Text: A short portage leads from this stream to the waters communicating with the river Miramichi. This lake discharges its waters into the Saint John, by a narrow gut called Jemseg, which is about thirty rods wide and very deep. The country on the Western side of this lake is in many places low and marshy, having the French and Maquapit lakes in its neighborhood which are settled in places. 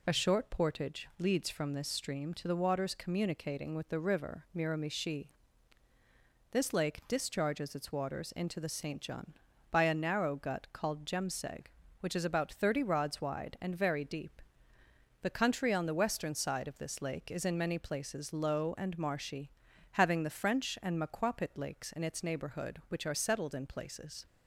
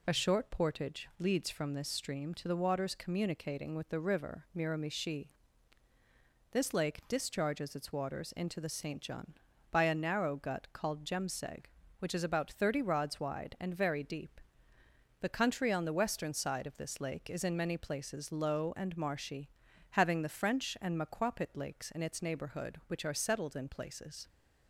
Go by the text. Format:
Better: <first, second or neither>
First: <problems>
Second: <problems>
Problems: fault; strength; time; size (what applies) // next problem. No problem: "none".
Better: neither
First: none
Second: none